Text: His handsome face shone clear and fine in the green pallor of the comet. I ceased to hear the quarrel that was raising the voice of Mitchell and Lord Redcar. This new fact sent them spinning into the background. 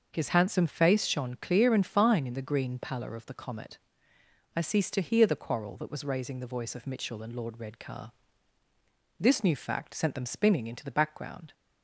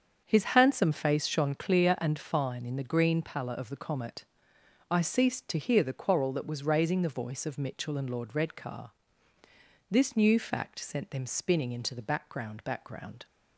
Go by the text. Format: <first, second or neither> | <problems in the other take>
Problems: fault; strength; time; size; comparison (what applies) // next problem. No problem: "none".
first | starts louder than the rest; until 1.2 s; 7 dB; also in the first // says "background" twice; at 12.6 s